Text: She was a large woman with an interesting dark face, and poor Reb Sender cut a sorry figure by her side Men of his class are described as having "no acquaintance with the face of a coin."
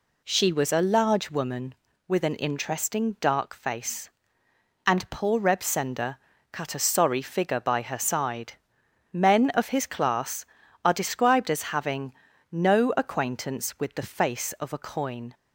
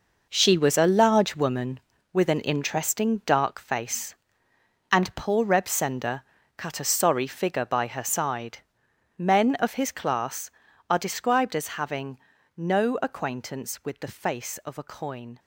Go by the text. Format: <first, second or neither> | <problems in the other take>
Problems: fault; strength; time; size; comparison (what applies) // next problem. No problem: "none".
first | gets quieter; strong; throughout; 11 dB // pauses between "Sender" and "cut"; slight; at 6.2 s; 0.34 s long; slight in the first // pauses between "side" and "Men"; noticeable; at 8.5 s; 0.58 s long; noticeable in the first // pauses between "having" and "no"; slight; at 12.1 s; 0.36 s long; slight in the first